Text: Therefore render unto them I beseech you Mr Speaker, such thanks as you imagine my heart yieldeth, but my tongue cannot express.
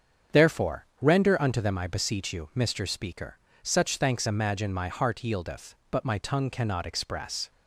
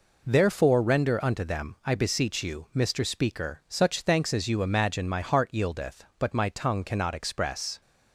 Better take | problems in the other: second | starts louder than the rest; strong; until 1.4 s; 7 dB // skips "as you"; at 4.2 s

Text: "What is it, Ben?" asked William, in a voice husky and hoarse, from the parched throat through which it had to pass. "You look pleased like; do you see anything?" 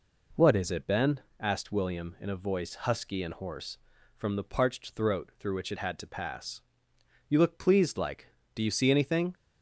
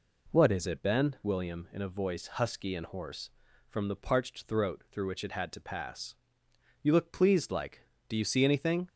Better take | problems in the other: first | skips "asked"; at 1.2 s

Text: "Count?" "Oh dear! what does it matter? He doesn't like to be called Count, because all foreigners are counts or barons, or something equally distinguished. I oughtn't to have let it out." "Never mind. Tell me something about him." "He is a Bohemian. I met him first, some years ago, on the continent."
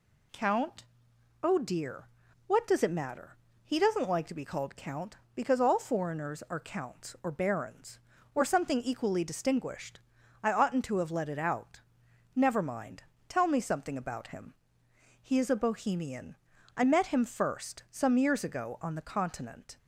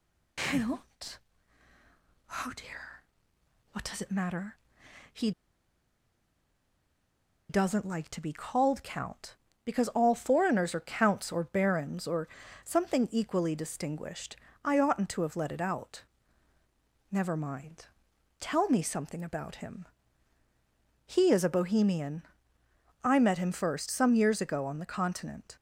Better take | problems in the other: first | pauses between "He" and "doesn't"; strong; at 5.3 s; 2.1 s long // pauses between "or" and "something"; slight; at 12.2 s; 0.34 s long

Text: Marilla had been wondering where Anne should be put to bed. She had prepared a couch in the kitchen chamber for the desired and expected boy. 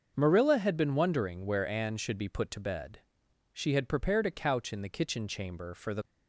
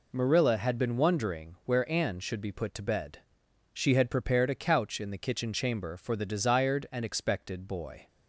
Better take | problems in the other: second | starts louder than the rest; until 1.1 s; 6 dB // stops before "desired and expected boy"; at 6.0 s

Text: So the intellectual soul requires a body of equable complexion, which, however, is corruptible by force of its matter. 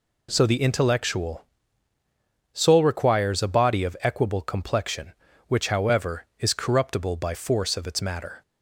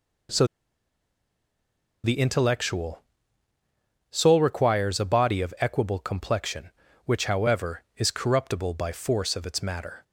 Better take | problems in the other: first | pauses between "So" and "the"; strong; at 0.4 s; 1.5 s long // pauses between "intellectual" and "soul"; at 3.0 s; 1.1 s long; also in the first

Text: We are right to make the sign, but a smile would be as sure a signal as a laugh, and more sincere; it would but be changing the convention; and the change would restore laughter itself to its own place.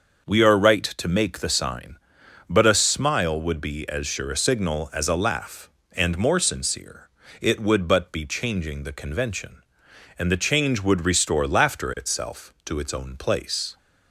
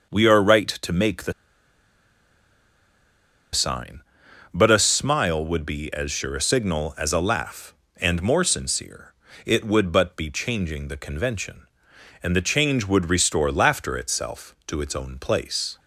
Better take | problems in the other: first | starts louder than the rest; until 1.1 s; 6 dB; also in the first // pauses between "the" and "sign"; strong; at 1.3 s; 2.2 s long

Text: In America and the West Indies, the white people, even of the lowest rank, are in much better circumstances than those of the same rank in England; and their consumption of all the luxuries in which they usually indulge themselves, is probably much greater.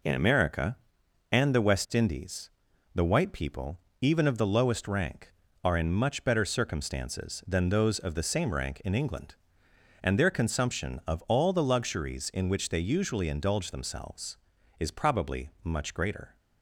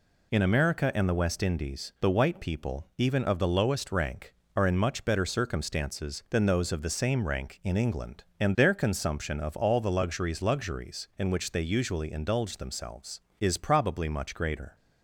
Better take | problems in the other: first | says "luxuries" twice; at 10.4 s

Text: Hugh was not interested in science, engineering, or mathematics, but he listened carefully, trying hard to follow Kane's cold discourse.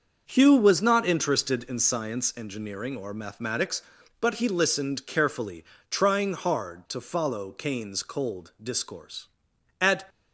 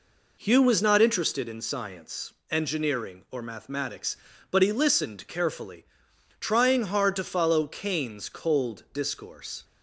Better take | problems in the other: second | starts louder than the rest; until 1.2 s; 6.5 dB // goes on to say "At"; slight; from 9.8 s on; 0.28 s long

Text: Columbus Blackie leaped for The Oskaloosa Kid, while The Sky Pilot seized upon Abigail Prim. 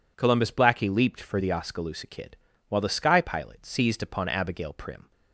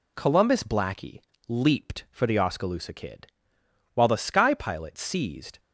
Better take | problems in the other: first | pauses between "Blackie" and "leaped"; slight; at 1.1 s; 0.28 s long // stops before "upon Abigail Prim"; at 5.5 s

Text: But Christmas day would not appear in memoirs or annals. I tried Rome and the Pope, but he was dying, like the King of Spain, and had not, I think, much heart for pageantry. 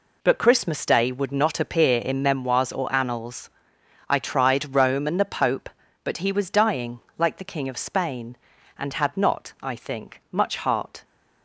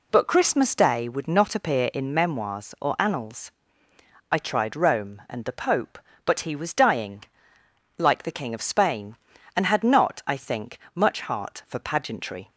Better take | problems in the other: second | stops before "for pageantry"; at 11.0 s

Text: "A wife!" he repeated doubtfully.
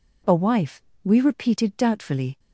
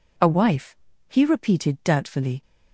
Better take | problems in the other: second | says "we" for "he"; at 1.0 s

